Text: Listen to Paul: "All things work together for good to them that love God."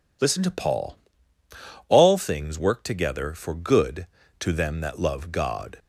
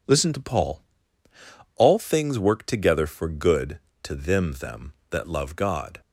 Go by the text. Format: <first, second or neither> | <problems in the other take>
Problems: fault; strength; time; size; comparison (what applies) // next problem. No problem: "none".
first | says "them" twice; at 4.5 s